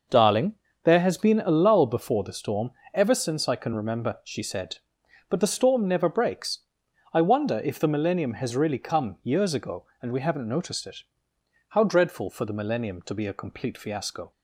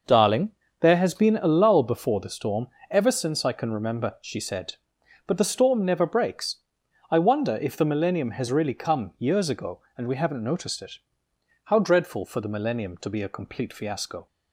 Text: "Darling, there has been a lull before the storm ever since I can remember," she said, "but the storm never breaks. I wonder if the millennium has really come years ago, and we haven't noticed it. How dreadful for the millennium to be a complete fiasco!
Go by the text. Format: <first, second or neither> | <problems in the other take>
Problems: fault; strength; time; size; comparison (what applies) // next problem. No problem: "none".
neither | pauses between "storm" and "ever"; slight; the same in both